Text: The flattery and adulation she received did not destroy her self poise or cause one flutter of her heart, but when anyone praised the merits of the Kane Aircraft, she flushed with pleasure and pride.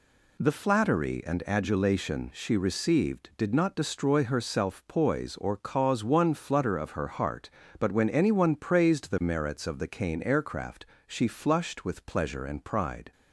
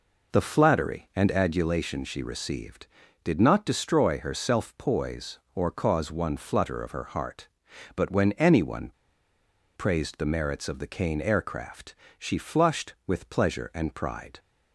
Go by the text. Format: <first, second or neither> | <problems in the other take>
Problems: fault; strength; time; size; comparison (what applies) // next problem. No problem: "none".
first | pauses between "anyone" and "praised"; noticeable; at 8.9 s; 0.83 s long